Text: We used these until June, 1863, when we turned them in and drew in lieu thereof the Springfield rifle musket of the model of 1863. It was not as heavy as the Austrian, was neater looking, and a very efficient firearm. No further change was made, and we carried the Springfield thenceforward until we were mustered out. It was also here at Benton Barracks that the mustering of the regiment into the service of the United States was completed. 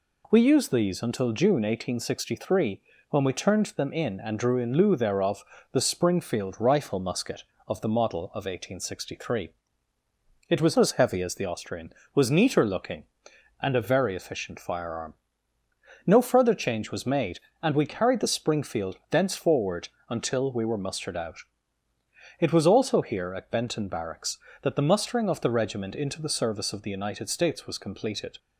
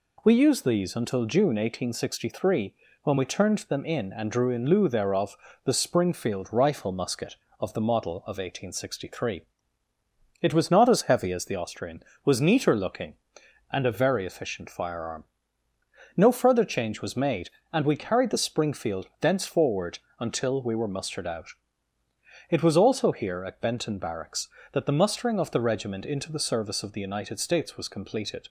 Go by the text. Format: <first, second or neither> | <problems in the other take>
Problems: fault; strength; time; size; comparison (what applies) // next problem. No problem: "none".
second | pauses between "thereof" and "the"; slight; at 5.4 s; 0.28 s long; slight in the second // skips "not"; at 10.7 s // pauses between "thenceforward" and "until"; slight; at 19.8 s; 0.18 s long; slight in the second